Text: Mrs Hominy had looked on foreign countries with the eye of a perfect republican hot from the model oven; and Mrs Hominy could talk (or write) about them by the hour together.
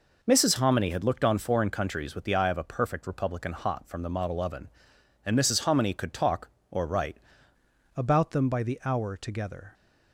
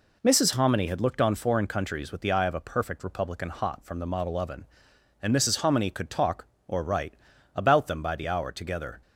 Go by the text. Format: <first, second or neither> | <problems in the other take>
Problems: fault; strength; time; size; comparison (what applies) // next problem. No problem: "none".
second | changes voice at "about"; from 7.9 s on; 1.8 s long